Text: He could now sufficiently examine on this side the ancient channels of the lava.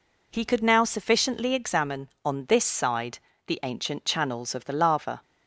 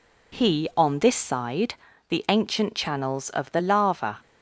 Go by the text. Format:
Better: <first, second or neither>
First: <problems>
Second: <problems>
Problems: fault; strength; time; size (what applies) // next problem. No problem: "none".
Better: first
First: pauses between "side" and "the"; slight; at 3.1 s; 0.28 s long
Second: skips "could now sufficiently examine"; at 0.7 s // pauses between "side" and "the"; slight; at 1.7 s; 0.34 s long